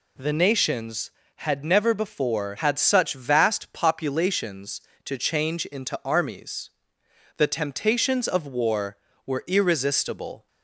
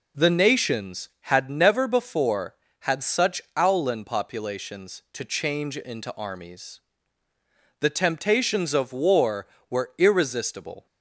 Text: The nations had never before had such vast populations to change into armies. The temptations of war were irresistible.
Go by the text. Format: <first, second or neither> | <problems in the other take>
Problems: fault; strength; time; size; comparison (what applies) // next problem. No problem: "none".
first | says "owlin" for "vast"; at 3.5 s